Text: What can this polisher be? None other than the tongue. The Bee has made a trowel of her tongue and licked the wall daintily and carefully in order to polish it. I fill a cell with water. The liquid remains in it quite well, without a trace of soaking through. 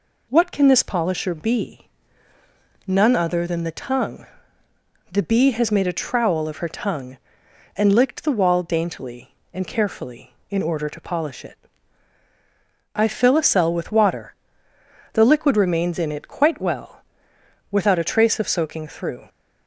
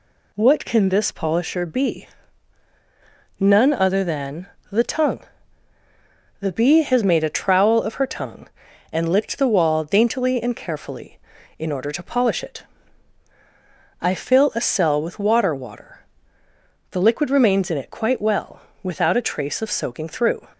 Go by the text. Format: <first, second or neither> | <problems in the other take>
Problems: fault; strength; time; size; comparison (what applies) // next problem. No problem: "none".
first | pauses between "than" and "the"; slight; at 4.4 s; 0.24 s long // says "water" twice; at 15.5 s